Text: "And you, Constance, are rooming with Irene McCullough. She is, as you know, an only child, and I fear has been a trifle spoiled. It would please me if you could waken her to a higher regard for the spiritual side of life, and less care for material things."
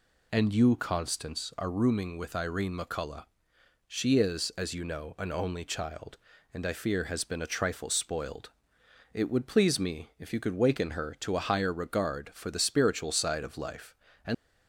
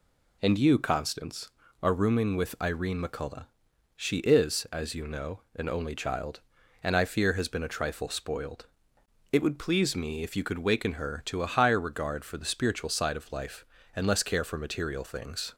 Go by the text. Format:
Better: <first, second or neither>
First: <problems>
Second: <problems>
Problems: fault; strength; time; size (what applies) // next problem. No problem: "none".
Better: second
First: stops before "less care for material things"; at 14.3 s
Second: none